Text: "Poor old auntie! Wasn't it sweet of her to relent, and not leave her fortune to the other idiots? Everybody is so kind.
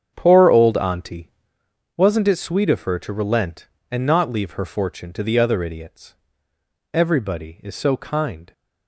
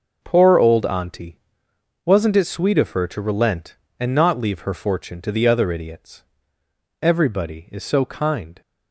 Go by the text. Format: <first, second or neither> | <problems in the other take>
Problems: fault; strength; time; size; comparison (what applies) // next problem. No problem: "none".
second | starts louder than the rest; strong; until 1.5 s; 8 dB